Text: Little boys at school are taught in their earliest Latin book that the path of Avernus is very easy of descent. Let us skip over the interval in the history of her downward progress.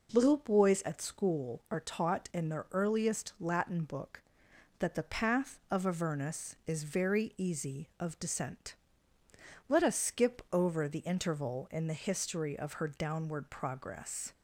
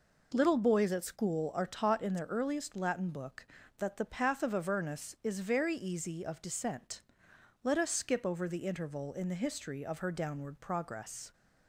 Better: neither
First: none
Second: none

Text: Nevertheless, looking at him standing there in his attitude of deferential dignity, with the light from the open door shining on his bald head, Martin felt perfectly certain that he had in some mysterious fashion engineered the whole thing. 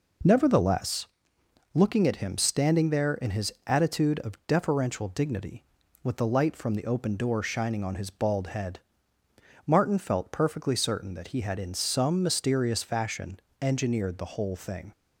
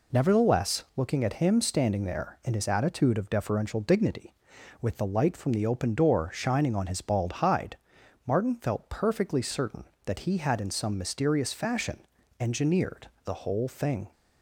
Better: first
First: pauses between "fashion" and "engineered"; slight; at 13.3 s; 0.20 s long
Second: says "hide" for "head"; at 7.3 s // pauses between "fashion" and "engineered"; at 12.0 s; 0.38 s long // pauses between "engineered" and "the"; slight; at 13.0 s; 0.16 s long

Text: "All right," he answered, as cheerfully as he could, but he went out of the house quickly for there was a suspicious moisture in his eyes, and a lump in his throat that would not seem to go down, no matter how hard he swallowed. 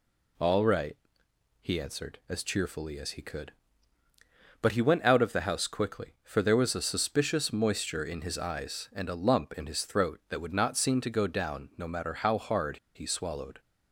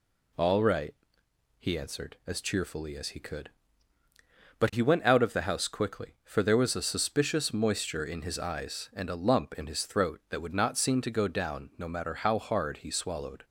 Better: second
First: pauses between "hard" and "he"; slight; at 12.7 s; 0.17 s long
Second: none

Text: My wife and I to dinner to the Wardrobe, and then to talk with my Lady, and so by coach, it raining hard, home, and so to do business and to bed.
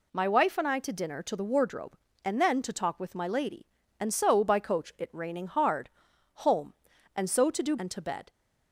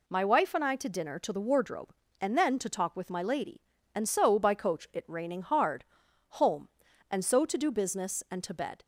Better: second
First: skips "business"; at 7.7 s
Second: none

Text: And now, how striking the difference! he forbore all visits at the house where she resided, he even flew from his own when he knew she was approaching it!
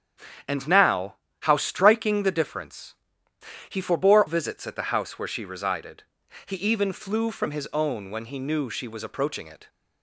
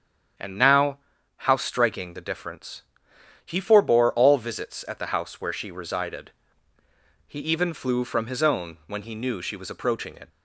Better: second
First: starts louder than the rest; strong; until 1.7 s; 8.5 dB // skips "all"; at 4.2 s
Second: starts louder than the rest; strong; until 1.7 s; 8 dB

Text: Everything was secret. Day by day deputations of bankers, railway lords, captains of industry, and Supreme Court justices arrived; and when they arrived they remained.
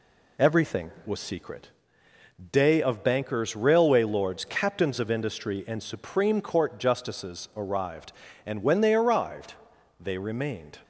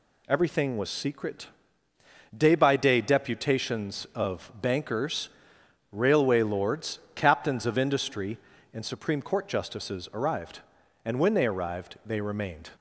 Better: second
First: skips "by day deputations"; at 2.8 s // pauses between "arrived" and "they"; at 9.5 s; 0.44 s long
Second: none

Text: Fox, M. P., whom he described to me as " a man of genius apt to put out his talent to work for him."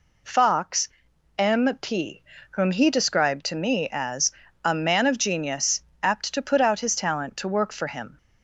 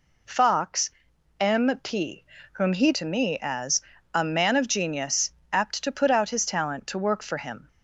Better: first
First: pauses between "genius" and "apt"; slight; at 5.8 s; 0.20 s long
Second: skips "described"; at 2.9 s // pauses between "genius" and "apt"; slight; at 5.3 s; 0.20 s long

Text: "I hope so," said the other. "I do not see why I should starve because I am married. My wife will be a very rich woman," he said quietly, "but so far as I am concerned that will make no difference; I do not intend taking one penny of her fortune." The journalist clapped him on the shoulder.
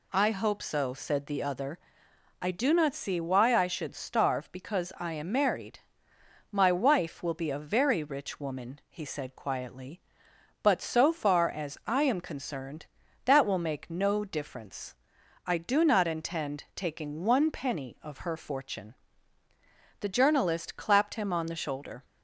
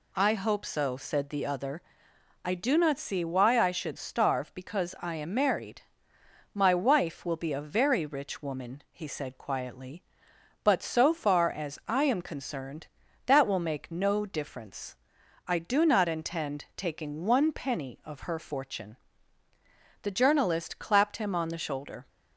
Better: neither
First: none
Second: none

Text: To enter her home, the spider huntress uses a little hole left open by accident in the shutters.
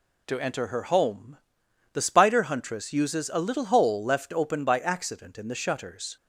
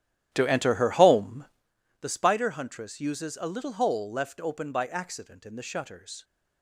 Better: first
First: none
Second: starts louder than the rest; strong; until 1.7 s; 12 dB

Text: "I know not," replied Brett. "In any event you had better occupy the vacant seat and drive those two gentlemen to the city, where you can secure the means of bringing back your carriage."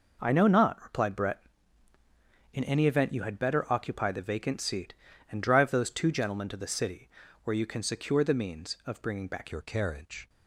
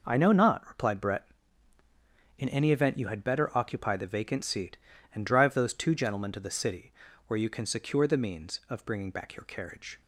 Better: second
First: changes voice at "your"; from 9.5 s on; 0.7 s long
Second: none

